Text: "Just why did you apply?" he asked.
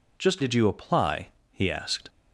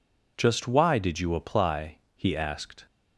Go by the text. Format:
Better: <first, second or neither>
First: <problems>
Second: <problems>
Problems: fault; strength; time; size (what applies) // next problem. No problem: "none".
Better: second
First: skips "why"; at 0.4 s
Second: none